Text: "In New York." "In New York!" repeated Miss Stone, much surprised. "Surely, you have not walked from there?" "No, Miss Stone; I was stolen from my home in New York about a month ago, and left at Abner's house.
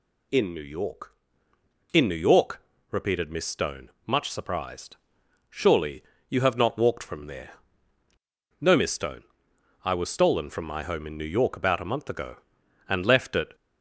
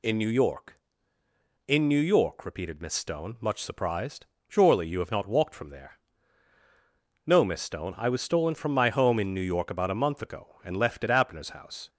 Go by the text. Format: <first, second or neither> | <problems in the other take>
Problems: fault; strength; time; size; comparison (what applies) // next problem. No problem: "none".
second | stops before "Abner's house"; at 13.5 s